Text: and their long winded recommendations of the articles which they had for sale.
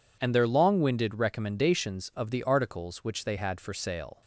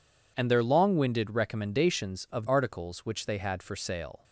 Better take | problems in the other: first | skips "the"; at 2.4 s

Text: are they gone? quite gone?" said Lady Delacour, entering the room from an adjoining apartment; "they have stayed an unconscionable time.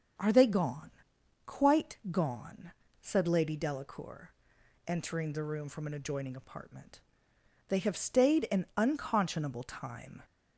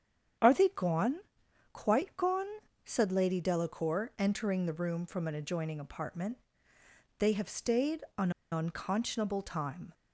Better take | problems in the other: first | starts louder than the rest; strong; until 1.9 s; 8.5 dB; also in the first // pauses between "an" and "unconscionable"; slight; at 8.2 s; 0.21 s long

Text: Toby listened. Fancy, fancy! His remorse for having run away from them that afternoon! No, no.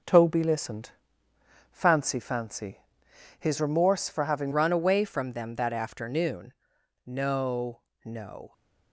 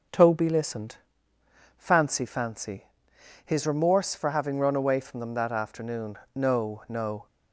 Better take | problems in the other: second | changes voice at "run"; from 4.5 s on; 4.0 s long

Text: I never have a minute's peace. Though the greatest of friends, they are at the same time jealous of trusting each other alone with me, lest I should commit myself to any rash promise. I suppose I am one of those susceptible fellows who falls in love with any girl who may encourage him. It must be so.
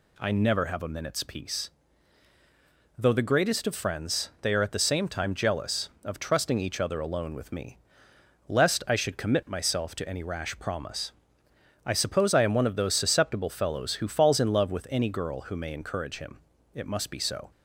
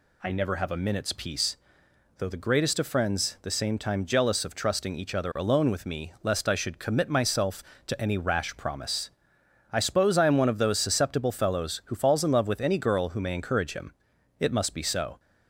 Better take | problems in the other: first | skips "they are at"; at 3.3 s

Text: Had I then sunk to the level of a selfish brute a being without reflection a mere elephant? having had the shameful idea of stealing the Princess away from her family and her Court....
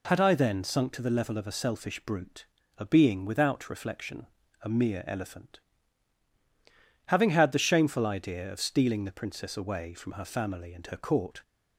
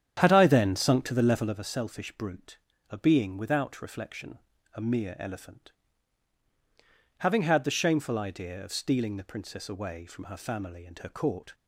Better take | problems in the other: first | starts louder than the rest; strong; until 1.7 s; 9 dB // pauses between "brute" and "a"; slight; at 2.5 s; 0.32 s long; slight in the first // pauses between "reflection" and "a"; slight; at 4.3 s; 0.36 s long; slight in the first

